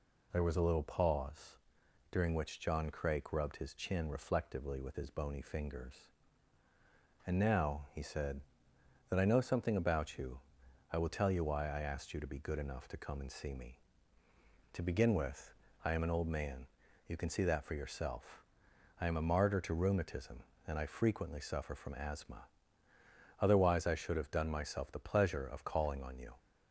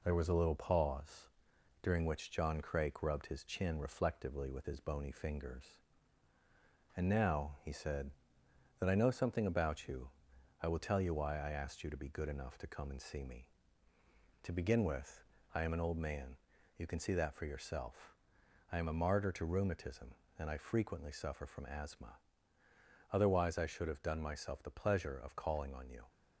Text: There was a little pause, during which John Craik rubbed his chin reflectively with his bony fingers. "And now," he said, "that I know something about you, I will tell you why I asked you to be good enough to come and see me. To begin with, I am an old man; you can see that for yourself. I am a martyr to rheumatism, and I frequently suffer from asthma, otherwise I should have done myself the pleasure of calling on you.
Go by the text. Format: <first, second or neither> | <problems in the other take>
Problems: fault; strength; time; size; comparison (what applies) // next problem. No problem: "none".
first | gets quieter; slight; throughout; 2.5 dB